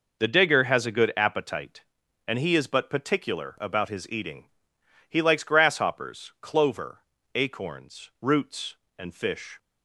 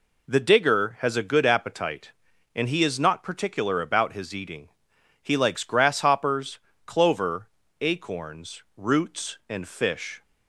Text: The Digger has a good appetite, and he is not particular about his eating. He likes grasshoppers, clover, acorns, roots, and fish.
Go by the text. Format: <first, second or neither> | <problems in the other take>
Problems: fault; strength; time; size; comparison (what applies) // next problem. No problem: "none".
second | says "but" for "not"; at 2.6 s